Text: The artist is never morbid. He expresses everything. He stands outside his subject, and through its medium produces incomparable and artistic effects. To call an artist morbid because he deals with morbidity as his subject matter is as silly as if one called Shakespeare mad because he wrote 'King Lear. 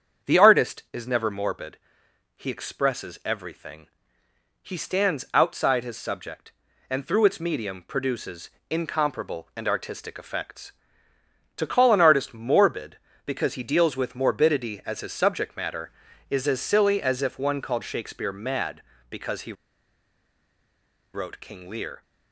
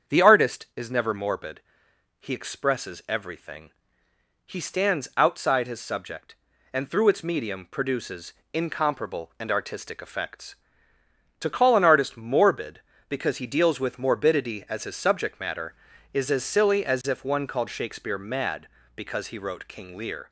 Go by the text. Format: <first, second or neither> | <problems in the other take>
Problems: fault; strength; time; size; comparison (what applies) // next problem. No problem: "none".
second | starts louder than the rest; strong; until 1.3 s; 7.5 dB; strong in the second // pauses between "produces" and "incomparable"; slight; at 8.4 s; 0.20 s long; slight in the second // pauses between "he" and "wrote"; strong; at 19.5 s; 1.6 s long